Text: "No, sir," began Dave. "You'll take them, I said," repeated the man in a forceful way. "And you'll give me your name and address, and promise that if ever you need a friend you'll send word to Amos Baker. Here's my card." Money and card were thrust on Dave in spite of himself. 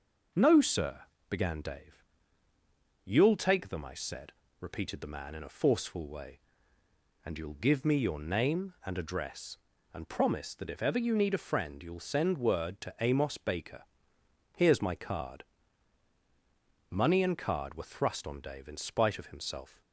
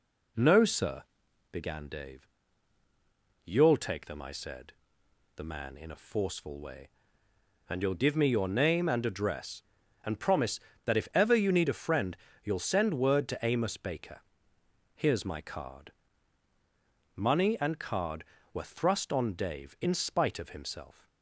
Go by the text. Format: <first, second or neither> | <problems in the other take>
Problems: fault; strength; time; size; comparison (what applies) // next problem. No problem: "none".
first | skips "repeated"; at 5.0 s // pauses between "friend" and "you'll"; slight; at 12.1 s; 0.28 s long